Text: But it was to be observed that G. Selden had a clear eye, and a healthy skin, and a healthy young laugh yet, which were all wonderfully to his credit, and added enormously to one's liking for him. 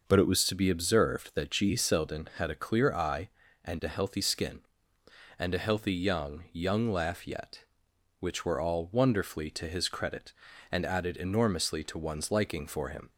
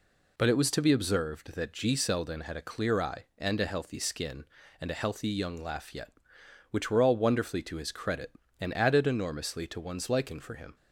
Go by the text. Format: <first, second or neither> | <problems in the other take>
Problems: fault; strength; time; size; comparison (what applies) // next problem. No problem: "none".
second | says "young" twice; at 6.5 s